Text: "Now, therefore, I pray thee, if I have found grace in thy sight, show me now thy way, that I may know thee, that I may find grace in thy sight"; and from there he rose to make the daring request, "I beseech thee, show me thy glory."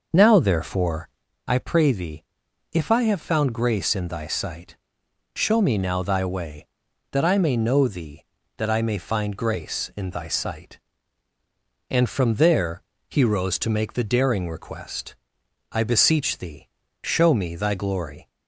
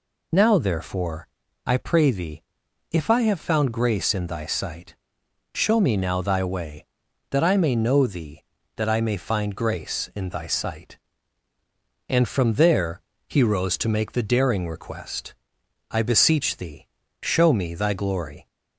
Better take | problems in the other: second | starts louder than the rest; noticeable; until 1.3 s; 6 dB // pauses between "there" and "he"; slight; at 12.8 s; 0.26 s long; slight in the second

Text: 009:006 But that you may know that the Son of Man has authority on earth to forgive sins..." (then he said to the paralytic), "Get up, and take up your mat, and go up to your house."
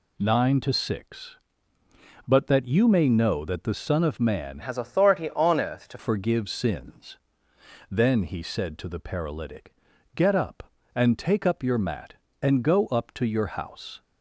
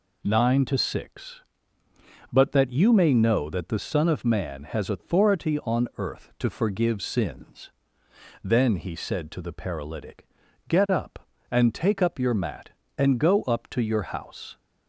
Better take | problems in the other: second | changes voice from "has" to "to"; from 4.6 to 5.9 s; 1.3 s long

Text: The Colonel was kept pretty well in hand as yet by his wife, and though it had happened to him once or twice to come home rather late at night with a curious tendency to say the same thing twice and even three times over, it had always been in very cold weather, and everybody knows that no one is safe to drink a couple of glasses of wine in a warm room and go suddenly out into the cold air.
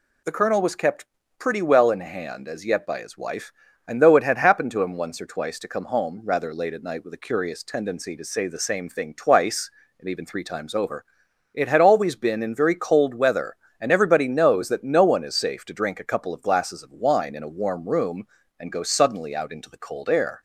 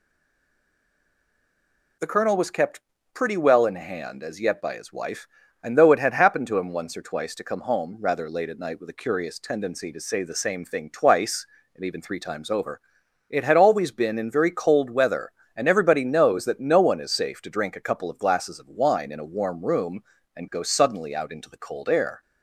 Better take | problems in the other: first | stays silent before the first word; noticeable; until 1.9 s; 1.9 s long // pauses between "kept" and "pretty"; slight; at 2.7 s; 0.34 s long; slight in the first

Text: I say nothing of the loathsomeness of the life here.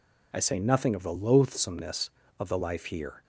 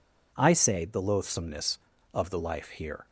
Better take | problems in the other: first | skips "nothing of"; at 0.8 s

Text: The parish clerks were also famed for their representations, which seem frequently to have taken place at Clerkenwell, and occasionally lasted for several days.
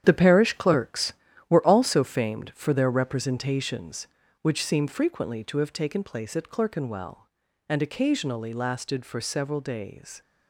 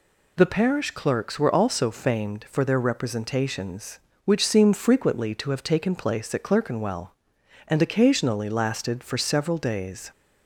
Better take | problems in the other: second | gets quieter; strong; throughout; 10 dB

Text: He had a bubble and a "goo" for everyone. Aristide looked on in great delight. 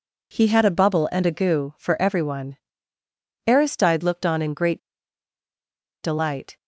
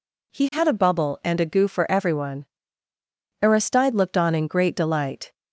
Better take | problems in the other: second | pauses between "great" and "delight"; at 4.7 s; 1.2 s long

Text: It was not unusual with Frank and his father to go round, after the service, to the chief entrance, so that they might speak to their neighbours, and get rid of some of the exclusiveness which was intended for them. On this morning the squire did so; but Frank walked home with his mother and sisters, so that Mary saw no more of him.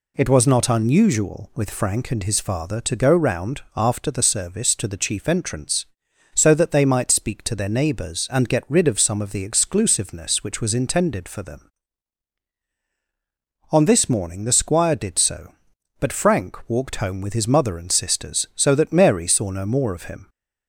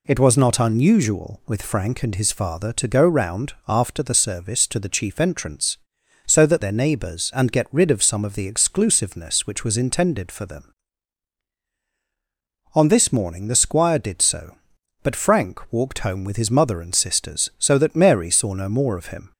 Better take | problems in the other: first | skips "they might speak to"; at 6.6 s

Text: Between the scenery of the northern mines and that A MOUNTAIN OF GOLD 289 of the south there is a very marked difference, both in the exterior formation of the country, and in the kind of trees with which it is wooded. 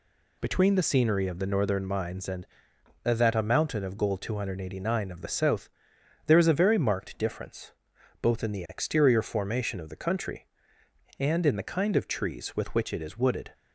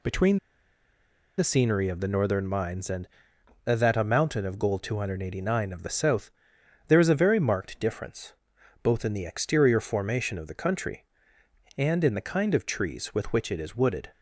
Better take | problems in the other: first | pauses between "Between" and "the"; at 0.3 s; 0.99 s long // pauses between "south" and "there"; noticeable; at 6.2 s; 0.60 s long; noticeable in the first

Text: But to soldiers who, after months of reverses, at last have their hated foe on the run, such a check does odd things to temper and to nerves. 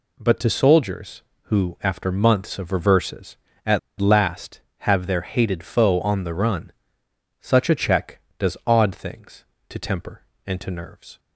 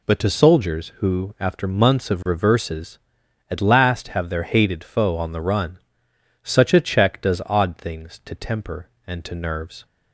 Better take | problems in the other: second | pauses between "at" and "last"; slight; at 3.7 s; 0.21 s long

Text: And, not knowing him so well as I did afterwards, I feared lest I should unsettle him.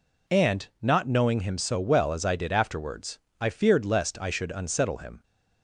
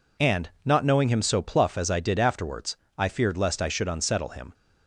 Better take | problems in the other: first | says "pluff" for "well"; at 1.4 s

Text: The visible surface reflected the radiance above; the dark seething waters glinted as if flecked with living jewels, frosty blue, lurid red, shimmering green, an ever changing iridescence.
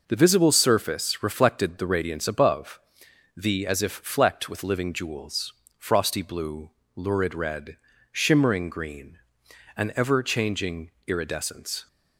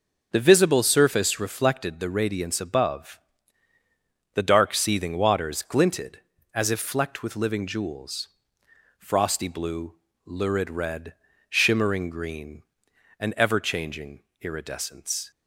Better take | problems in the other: second | skips "dark seething waters glinted"; at 3.6 s // pauses between "changing" and "iridescence"; slight; at 10.9 s; 0.16 s long; slight in the second

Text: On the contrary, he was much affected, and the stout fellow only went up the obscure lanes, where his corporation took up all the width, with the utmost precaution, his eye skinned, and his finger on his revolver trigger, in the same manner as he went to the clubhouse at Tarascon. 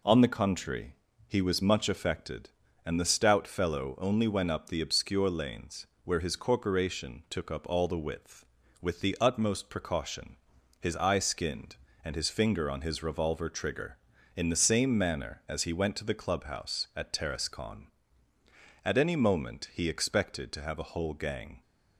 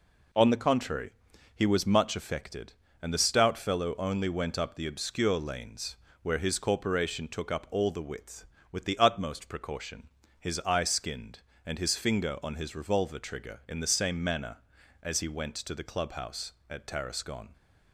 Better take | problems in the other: second | goes on to say "At any moment he expected to have a whole gang"; strong; from 18.8 s on; 2.7 s long

